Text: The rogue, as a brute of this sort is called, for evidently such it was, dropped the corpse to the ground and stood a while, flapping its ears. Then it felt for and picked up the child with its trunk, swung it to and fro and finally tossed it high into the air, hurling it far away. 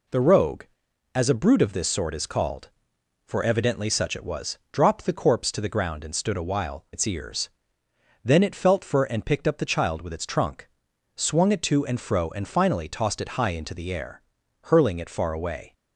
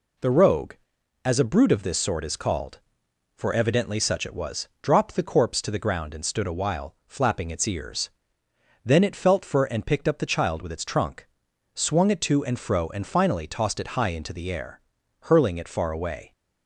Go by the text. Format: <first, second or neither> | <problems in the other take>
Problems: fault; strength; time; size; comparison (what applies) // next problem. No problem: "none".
second | skips "flapping"; at 6.8 s